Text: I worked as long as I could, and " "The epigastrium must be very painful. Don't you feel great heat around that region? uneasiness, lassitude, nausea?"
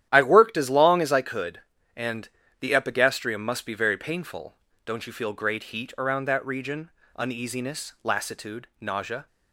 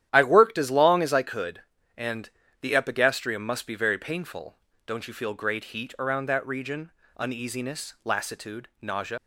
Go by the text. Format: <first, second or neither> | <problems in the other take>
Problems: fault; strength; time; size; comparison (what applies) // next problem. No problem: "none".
first | starts louder than the rest; strong; until 1.1 s; 11.5 dB; strong in the first // leaves "nausea" unfinished; at 9.1 s; 90 ms